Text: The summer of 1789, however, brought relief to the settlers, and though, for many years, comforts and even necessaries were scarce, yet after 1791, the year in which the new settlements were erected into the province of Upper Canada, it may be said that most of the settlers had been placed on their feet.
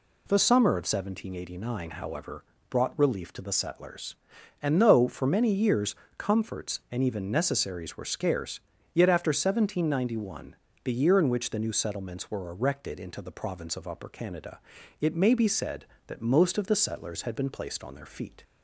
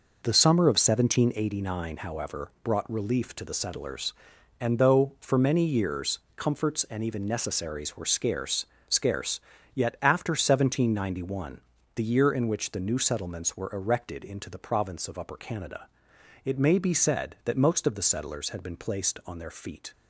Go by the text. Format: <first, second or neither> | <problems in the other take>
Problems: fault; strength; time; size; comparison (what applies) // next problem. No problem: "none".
first | says "scarce" twice; at 8.8 s